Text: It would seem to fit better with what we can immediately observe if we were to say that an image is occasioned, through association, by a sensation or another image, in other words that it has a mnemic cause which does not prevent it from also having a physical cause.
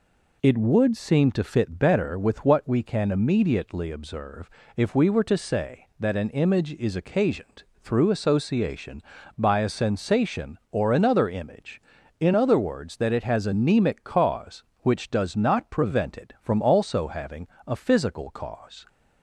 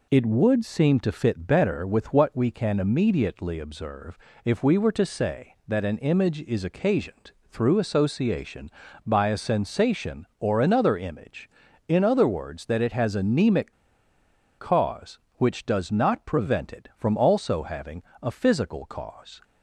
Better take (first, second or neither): first